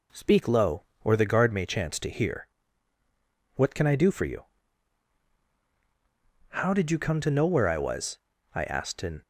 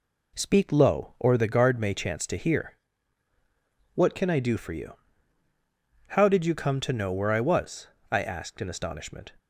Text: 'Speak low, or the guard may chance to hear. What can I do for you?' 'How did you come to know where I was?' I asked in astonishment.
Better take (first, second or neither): second